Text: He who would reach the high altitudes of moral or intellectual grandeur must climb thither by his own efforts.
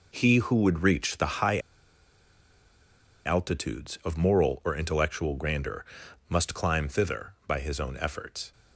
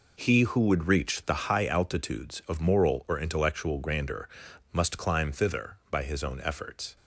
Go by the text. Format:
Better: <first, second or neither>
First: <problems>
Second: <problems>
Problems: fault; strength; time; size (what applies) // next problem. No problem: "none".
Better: second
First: pauses between "high" and "altitudes"; strong; at 1.5 s; 1.6 s long // pauses between "grandeur" and "must"; noticeable; at 5.8 s; 0.46 s long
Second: pauses between "grandeur" and "must"; noticeable; at 4.2 s; 0.46 s long